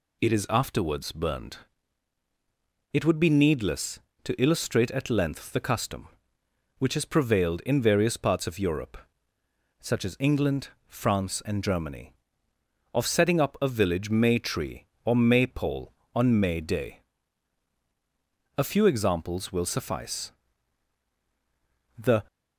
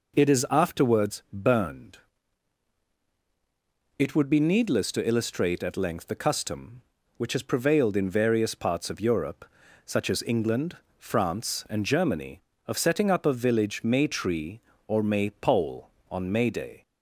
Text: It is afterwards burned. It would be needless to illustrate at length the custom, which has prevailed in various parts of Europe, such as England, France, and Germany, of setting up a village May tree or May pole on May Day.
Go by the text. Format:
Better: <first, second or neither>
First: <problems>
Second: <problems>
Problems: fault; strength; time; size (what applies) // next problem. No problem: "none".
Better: second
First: goes on to say "A few examples will suffice The"; strong; from 18.5 s on; 3.7 s long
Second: none